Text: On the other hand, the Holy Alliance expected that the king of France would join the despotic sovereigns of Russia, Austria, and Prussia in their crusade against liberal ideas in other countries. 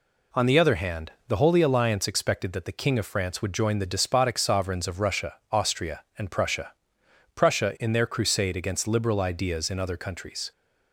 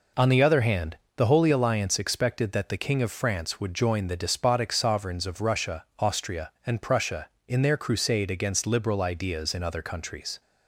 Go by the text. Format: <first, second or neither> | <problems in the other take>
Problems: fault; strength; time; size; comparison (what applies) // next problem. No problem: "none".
second | says "Prussia" twice; at 7.3 s